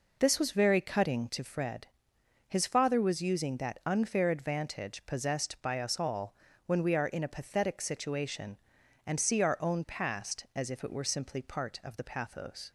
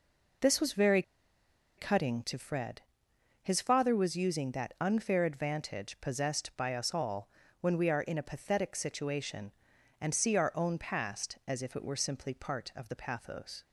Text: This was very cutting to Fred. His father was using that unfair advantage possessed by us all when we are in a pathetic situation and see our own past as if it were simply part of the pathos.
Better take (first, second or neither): first